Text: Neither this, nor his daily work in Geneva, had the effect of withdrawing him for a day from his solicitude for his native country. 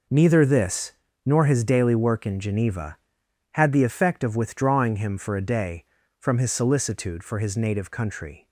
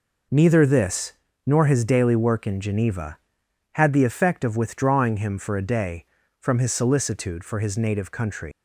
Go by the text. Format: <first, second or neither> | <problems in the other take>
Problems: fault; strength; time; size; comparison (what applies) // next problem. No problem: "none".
first | leaves "country" unfinished; at 8.5 s; 170 ms